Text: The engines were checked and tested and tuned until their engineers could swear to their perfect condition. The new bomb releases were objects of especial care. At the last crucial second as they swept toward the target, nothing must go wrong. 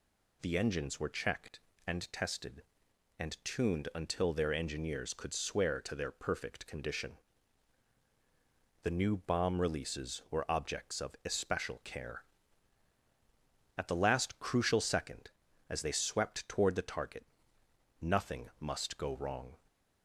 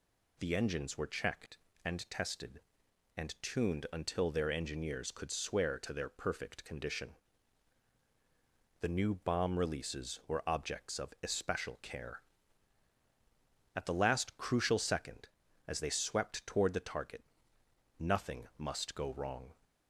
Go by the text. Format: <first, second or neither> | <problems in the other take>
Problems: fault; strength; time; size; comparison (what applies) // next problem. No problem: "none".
neither | none